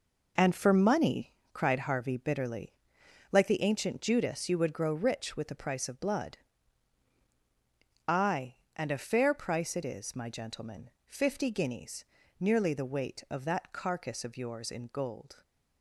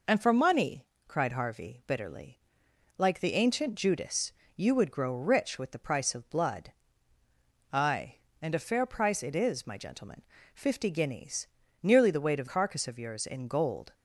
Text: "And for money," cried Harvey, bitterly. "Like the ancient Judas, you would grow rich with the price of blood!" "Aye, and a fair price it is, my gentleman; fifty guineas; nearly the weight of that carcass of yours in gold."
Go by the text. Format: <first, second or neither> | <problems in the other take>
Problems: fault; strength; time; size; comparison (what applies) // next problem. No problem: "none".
first | skips "that"; at 12.4 s